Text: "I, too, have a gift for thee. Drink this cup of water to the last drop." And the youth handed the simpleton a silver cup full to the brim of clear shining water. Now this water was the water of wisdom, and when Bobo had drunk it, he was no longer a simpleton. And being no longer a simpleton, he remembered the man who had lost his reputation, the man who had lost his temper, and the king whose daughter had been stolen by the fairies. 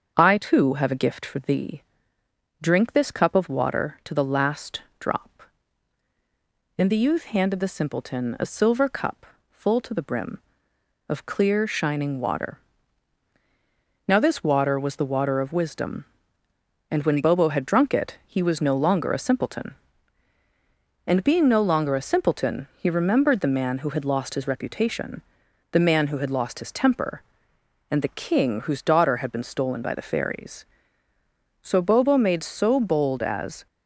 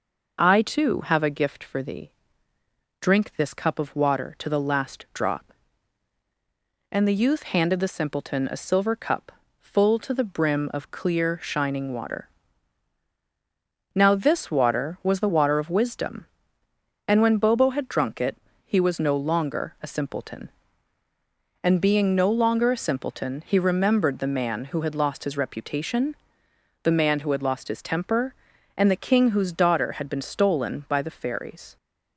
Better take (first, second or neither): second